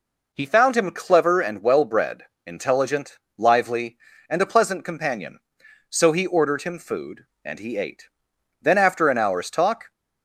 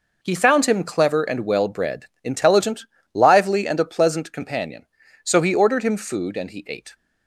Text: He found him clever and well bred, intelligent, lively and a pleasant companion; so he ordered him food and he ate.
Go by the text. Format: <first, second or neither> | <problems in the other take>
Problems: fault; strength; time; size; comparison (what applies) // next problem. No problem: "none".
second | goes on to say "Then after an hour's talk"; from 8.5 s on; 1.3 s long